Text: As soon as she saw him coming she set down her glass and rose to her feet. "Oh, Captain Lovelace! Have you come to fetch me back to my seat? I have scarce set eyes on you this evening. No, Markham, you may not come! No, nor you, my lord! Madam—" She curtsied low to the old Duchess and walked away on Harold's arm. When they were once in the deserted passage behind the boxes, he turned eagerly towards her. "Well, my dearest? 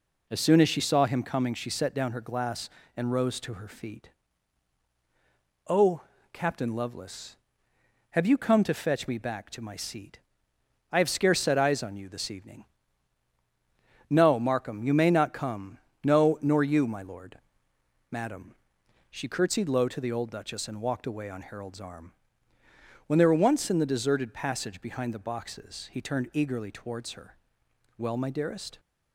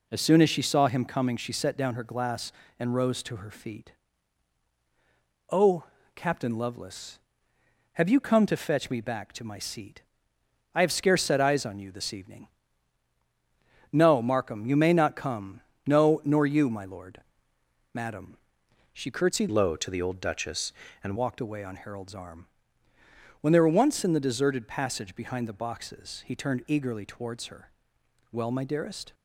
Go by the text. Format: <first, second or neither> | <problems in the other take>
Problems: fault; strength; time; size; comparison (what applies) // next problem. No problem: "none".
first | changes voice from "low" to "and"; from 19.5 to 21.1 s; 1.6 s long